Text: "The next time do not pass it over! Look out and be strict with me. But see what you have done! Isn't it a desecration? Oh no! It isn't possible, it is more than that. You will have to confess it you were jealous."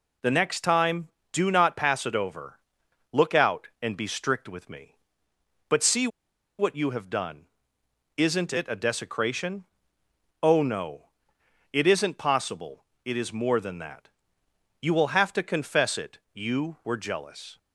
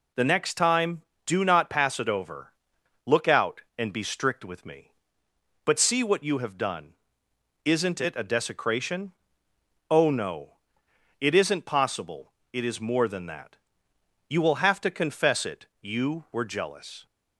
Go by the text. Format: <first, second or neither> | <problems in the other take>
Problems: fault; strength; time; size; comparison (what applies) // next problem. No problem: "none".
second | pauses between "see" and "what"; noticeable; at 6.0 s; 0.51 s long // pauses between "it" and "you"; slight; at 16.1 s; 0.16 s long; slight in the second